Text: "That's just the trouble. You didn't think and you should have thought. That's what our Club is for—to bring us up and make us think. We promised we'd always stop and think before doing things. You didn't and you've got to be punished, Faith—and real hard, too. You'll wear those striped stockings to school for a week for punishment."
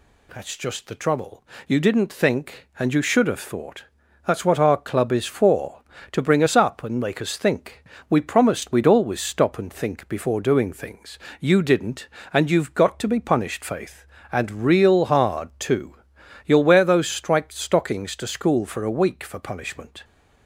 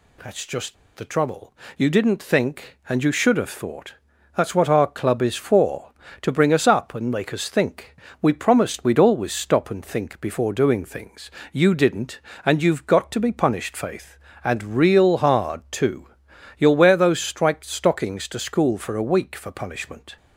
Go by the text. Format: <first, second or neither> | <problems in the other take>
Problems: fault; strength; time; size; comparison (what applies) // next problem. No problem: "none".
first | pauses between "just" and "the"; slight; at 0.7 s; 0.20 s long